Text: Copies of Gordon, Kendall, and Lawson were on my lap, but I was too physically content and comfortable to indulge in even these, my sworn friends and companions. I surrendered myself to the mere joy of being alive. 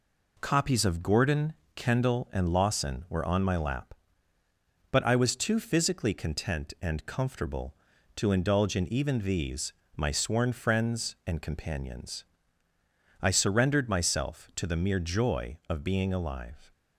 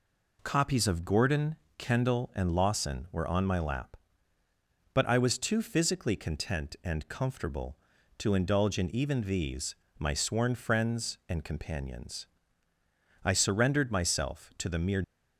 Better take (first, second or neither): first